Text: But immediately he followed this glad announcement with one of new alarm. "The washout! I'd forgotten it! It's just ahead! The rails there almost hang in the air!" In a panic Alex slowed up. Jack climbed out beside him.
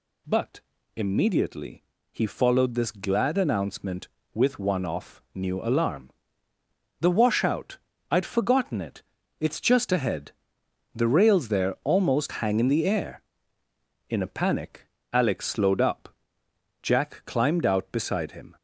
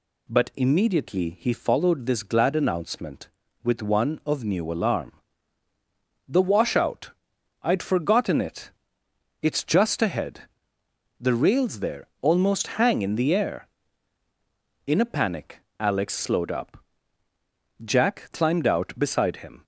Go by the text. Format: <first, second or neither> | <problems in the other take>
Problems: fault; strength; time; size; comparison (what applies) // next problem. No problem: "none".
second | pauses between "But" and "immediately"; slight; at 0.6 s; 0.36 s long // pauses between "immediately" and "he"; slight; at 1.8 s; 0.30 s long // says "off" for "of"; at 4.8 s // pauses between "panic" and "Alex"; slight; at 14.8 s; 0.26 s long; slight in the second